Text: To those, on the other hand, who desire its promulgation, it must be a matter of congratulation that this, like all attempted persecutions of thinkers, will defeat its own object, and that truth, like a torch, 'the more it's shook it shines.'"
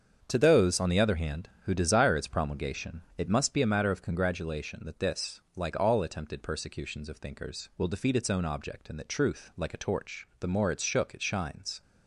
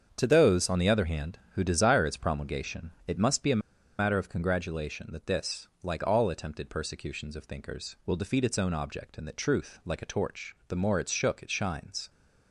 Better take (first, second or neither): first